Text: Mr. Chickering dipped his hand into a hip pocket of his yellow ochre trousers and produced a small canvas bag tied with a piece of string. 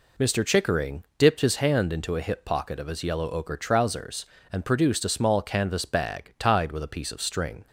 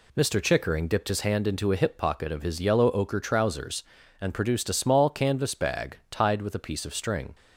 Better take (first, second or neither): neither